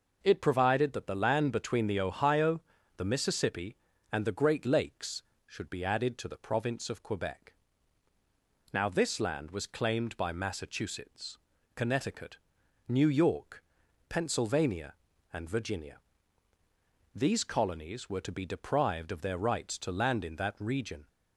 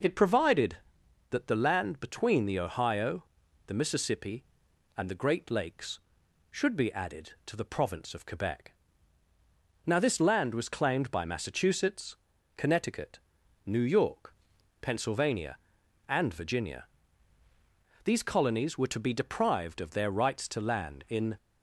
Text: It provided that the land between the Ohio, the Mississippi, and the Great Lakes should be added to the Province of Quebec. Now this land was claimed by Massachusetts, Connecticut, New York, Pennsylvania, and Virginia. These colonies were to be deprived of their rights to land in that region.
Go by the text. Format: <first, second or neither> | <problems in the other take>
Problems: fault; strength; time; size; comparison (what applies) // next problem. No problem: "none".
first | stops before "that region"; at 21.3 s